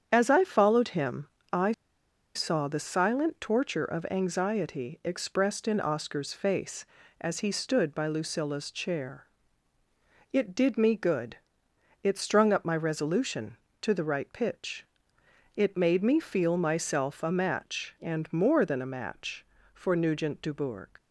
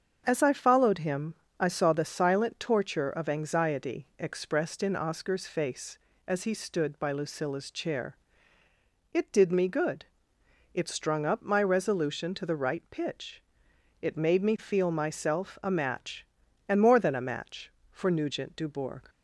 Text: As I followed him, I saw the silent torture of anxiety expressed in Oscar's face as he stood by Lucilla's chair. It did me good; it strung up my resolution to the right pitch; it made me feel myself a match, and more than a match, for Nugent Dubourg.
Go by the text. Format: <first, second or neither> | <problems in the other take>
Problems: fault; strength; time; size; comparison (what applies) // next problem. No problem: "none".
second | starts louder than the rest; strong; until 1.1 s; 8 dB; also in the second // pauses between "I" and "saw"; noticeable; at 1.7 s; 0.62 s long